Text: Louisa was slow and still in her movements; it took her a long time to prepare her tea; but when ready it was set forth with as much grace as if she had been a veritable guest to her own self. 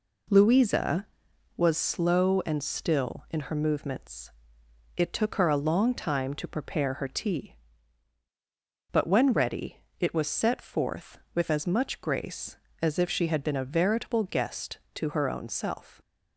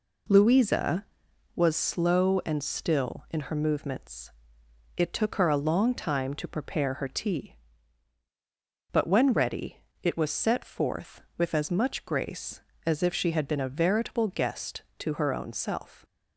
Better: neither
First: pauses between "ready" and "it"; slight; at 9.7 s; 0.24 s long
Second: pauses between "ready" and "it"; slight; at 9.7 s; 0.27 s long

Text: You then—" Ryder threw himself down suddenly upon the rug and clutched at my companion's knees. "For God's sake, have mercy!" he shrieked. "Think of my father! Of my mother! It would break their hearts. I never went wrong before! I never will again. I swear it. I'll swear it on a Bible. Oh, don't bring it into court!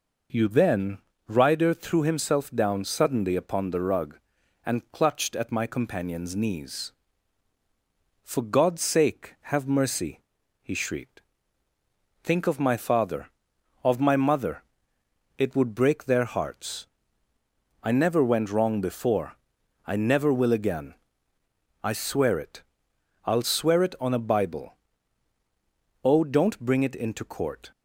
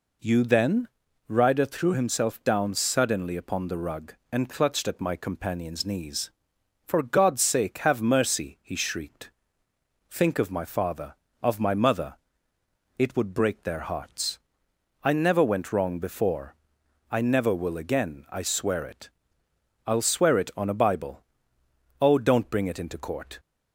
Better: neither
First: none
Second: none

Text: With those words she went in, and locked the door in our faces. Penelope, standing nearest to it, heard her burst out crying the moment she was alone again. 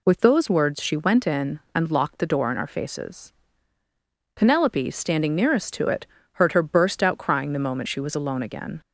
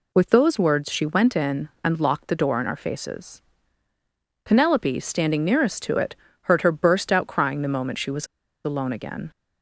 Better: first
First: none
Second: pauses between "was" and "alone"; at 8.2 s; 0.38 s long

